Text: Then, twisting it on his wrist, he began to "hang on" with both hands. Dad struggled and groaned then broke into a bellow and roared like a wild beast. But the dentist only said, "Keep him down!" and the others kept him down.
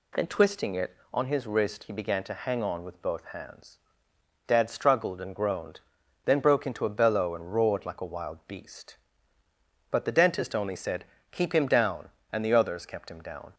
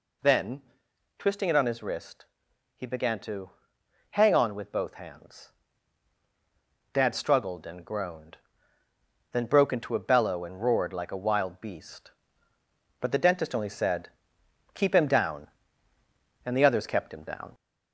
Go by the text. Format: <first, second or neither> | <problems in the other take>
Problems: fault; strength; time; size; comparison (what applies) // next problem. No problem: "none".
first | gets louder; slight; throughout; 2.5 dB // pauses between "to" and "hang"; noticeable; at 3.5 s; 0.58 s long // pauses between "groaned" and "then"; noticeable; at 8.3 s; 0.96 s long; also in the first